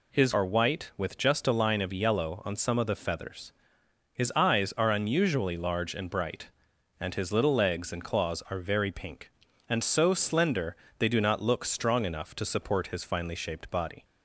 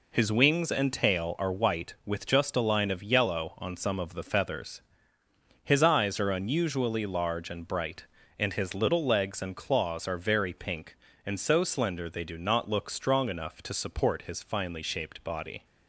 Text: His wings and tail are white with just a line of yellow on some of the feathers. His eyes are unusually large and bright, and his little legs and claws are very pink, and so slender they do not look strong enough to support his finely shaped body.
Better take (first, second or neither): second